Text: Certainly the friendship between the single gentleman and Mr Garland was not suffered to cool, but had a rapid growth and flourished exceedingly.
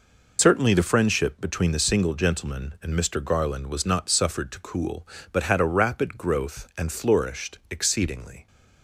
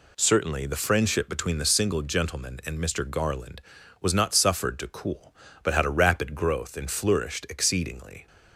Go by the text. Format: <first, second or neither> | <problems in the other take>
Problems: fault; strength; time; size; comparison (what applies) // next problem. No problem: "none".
second | loses the start of "Certainly"; at 0.3 s; 75 ms